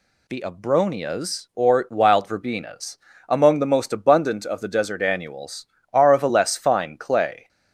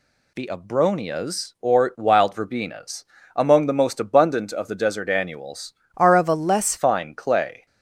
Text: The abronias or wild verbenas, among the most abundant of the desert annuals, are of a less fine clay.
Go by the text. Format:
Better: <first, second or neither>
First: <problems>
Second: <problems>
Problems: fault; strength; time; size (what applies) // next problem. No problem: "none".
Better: first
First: none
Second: changes voice from "are" to "less"; from 5.9 to 6.7 s; 0.8 s long